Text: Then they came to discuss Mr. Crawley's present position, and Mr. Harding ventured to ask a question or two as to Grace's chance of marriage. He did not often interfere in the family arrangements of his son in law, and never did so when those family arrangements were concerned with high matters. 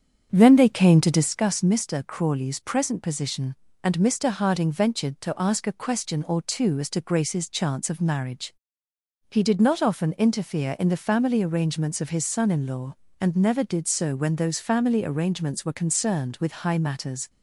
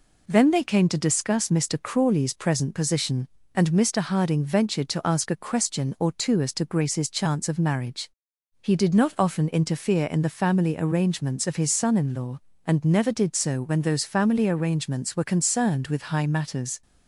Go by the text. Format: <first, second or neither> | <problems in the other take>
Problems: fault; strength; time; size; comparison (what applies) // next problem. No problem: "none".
second | starts louder than the rest; strong; until 1.3 s; 8 dB